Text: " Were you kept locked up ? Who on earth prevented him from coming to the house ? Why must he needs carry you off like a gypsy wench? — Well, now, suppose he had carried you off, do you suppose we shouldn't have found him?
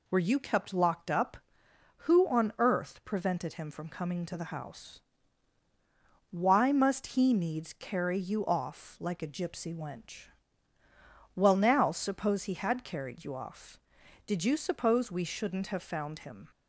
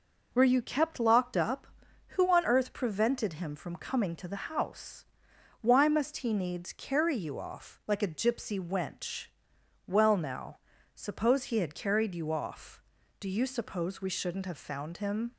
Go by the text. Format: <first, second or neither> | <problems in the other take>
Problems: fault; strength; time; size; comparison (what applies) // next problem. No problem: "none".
second | says "did" for "do"; at 14.2 s